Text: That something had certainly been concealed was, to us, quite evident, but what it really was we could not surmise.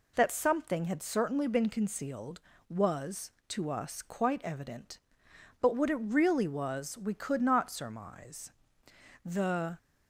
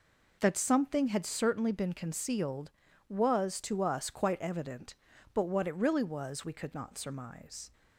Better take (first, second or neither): second